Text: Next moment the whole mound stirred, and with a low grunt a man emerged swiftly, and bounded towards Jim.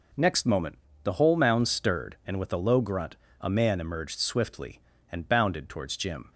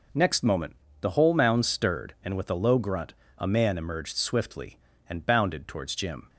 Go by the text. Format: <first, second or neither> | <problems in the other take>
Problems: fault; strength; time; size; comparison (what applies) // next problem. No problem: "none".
neither | pauses between "moment" and "the"; slight; the same in both // pauses between "grunt" and "a"; slight; the same in both